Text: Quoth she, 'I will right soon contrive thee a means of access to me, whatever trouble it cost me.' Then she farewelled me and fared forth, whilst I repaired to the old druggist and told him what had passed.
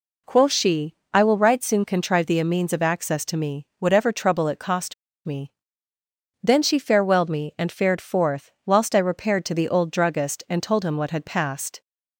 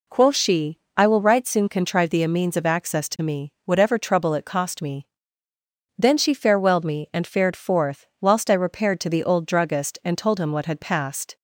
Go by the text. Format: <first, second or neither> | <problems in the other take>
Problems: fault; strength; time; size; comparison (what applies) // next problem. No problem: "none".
second | pauses between "cost" and "me"; slight; at 4.9 s; 0.32 s long